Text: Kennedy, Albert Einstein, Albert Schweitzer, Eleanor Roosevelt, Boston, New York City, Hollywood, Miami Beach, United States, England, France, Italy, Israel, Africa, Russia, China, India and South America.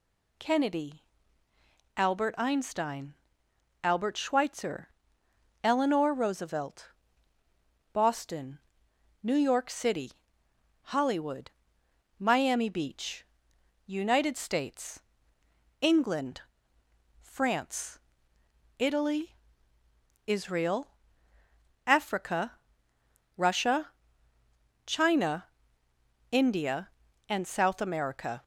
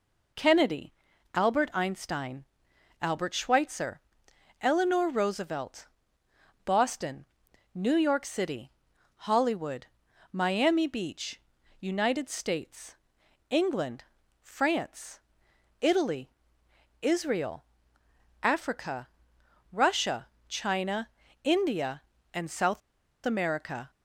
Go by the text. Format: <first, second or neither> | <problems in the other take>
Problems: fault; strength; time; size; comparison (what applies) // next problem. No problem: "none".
first | pauses between "South" and "America"; at 22.8 s; 0.45 s long